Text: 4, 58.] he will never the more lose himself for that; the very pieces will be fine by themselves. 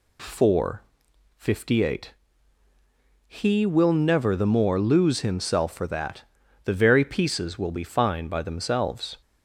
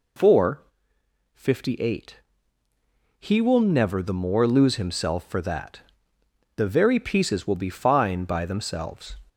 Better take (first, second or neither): neither